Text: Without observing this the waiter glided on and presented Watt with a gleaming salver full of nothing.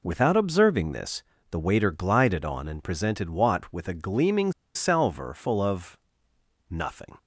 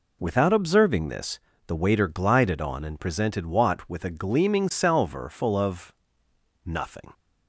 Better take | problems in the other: second | pauses between "this" and "the"; slight; at 1.2 s; 0.26 s long; slight in the second // pauses between "gleaming" and "salver"; slight; at 4.5 s; 0.23 s long // pauses between "of" and "nothing"; noticeable; at 5.9 s; 0.72 s long; noticeable in the second

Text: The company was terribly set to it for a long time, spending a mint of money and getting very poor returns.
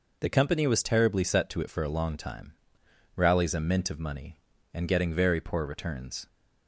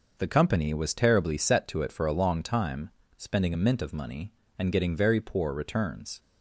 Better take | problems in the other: second | says "rallies" for "spending"; at 3.1 s

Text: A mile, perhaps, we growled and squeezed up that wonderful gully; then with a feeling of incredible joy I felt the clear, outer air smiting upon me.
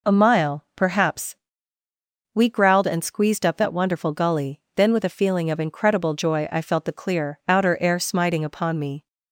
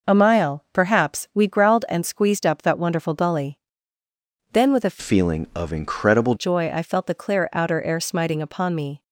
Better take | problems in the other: first | changes voice from "feeling" to "incredible"; from 4.9 to 6.3 s; 1.4 s long

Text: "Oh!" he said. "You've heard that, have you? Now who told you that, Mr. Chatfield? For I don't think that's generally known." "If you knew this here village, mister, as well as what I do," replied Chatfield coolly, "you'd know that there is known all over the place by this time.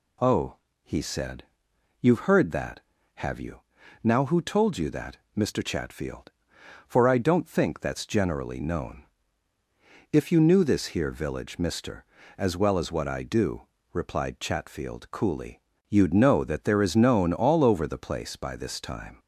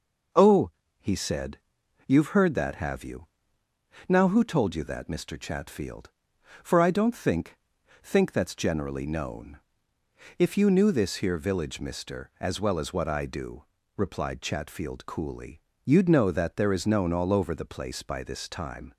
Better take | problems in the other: first | says "think" twice; at 8.0 s

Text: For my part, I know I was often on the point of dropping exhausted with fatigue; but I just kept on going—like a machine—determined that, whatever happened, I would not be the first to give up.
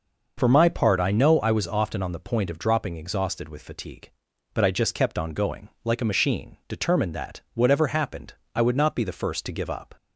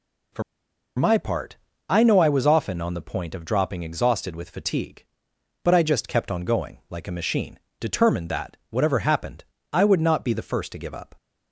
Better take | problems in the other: first | pauses between "For" and "my"; noticeable; at 0.4 s; 0.54 s long

